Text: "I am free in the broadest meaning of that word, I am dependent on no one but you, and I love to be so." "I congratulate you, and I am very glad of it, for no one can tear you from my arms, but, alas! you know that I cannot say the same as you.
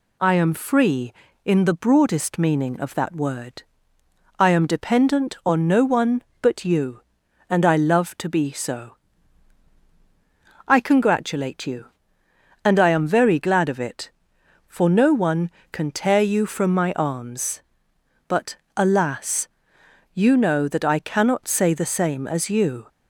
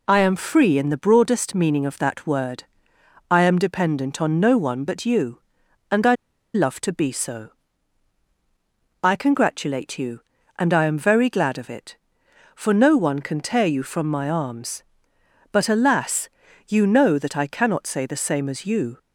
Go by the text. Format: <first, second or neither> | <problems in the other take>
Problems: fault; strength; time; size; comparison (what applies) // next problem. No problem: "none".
first | pauses between "I" and "love"; at 6.1 s; 0.41 s long